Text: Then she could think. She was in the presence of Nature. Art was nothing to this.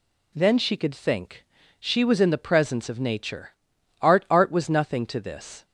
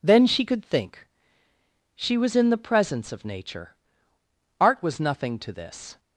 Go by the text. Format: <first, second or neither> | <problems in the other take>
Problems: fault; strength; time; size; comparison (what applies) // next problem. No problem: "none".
second | says "Art" twice; at 4.3 s